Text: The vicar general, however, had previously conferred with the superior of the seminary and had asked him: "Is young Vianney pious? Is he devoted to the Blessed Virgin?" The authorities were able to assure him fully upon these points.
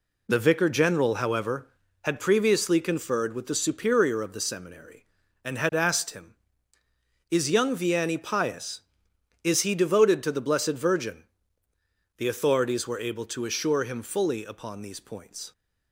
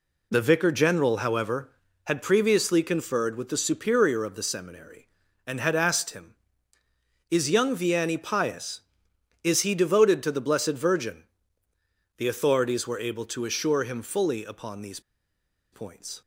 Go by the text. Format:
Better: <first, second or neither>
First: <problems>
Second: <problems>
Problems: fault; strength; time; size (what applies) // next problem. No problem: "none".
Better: first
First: none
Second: pauses between "these" and "points"; noticeable; at 14.9 s; 0.72 s long